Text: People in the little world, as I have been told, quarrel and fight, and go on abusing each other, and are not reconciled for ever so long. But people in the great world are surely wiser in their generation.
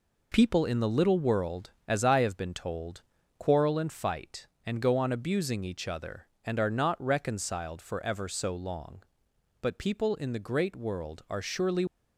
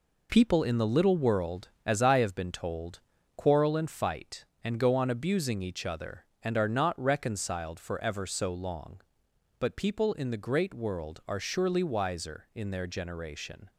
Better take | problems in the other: second | stops before "wiser in their generation"; at 11.8 s

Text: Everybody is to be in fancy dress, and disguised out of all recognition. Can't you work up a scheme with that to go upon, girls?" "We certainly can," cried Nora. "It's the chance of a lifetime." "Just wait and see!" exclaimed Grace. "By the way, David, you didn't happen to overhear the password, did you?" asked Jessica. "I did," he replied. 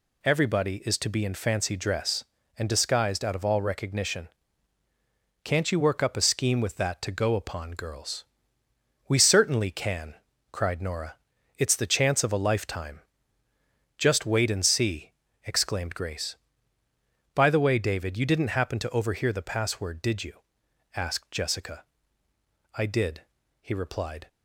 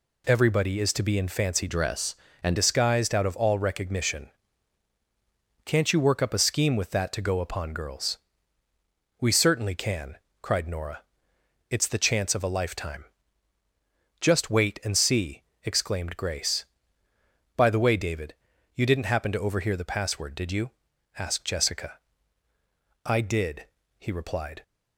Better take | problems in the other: first | changes voice from "dress" to "and"; from 1.6 to 2.5 s; 0.9 s long

